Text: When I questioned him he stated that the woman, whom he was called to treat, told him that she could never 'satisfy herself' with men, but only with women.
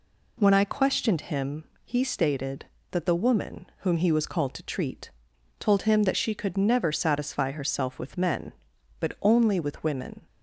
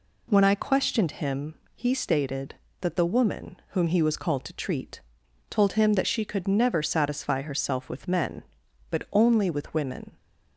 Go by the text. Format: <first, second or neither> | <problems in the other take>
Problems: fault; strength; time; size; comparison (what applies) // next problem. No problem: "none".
neither | pauses between "him" and "he"; slight; the same in both